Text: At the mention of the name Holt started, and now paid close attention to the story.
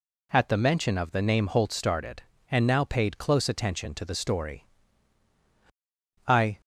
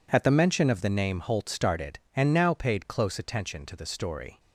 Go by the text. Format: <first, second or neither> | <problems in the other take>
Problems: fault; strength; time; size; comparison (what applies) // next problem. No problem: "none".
second | goes on to say "I"; slight; from 6.2 s on; 0.32 s long